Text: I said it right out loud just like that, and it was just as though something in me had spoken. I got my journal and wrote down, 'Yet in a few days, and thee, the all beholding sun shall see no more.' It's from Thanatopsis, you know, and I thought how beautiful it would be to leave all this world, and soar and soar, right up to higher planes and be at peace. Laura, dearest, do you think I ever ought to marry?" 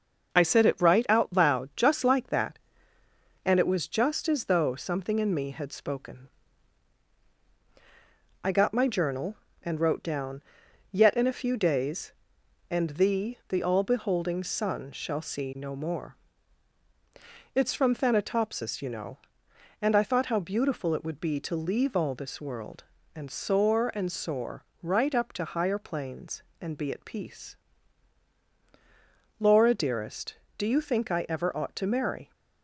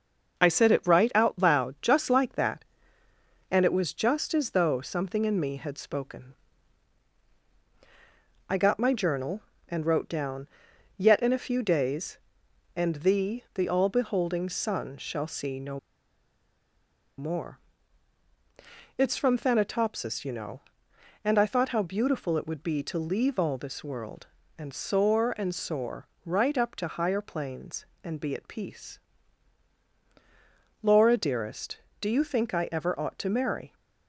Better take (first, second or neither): first